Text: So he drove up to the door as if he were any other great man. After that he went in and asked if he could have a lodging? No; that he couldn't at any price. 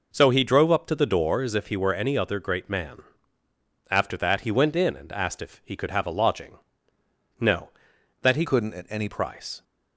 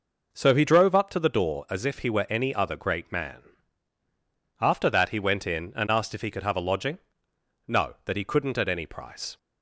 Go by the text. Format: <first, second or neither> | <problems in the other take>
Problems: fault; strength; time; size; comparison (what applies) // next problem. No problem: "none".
second | changes voice from "couldn't" to "any"; from 8.4 to 9.0 s; 0.6 s long